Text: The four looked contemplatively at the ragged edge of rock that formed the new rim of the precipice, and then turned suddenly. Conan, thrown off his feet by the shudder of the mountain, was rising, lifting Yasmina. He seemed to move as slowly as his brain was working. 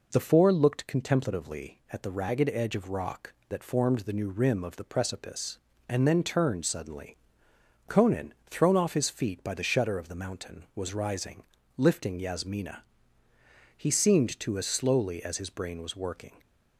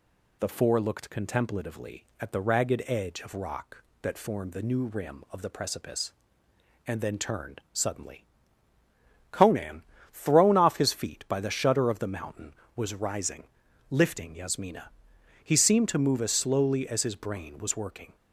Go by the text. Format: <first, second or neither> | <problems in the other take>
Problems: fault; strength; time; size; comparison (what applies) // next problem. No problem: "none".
second | skips "move"; at 14.5 s